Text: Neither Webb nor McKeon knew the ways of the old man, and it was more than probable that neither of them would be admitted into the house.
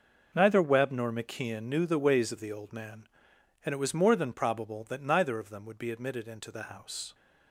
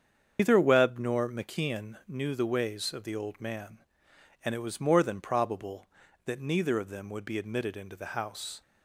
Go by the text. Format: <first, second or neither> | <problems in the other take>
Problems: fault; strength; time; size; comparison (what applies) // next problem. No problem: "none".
first | loses the start of "Neither"; at 0.3 s; 145 ms // starts louder than the rest; strong; until 1.4 s; 7.5 dB